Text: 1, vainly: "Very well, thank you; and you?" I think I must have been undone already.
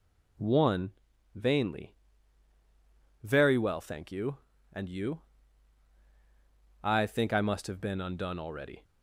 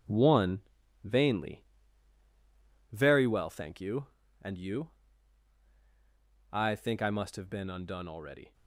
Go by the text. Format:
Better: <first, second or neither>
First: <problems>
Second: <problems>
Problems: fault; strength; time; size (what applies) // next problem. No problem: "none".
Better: first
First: none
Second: gets quieter; strong; throughout; 7.5 dB